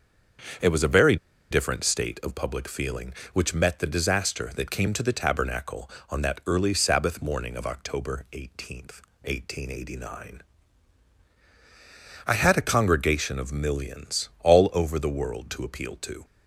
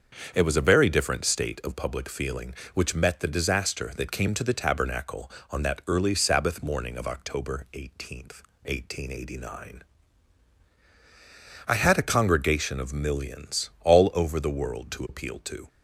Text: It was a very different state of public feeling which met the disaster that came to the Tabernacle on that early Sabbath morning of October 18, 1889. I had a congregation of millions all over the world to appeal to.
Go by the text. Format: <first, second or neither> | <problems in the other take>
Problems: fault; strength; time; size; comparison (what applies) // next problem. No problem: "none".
second | starts louder than the rest; strong; until 1.9 s; 7 dB; strong in the second // pauses between "very" and "different"; slight; at 1.1 s; 0.35 s long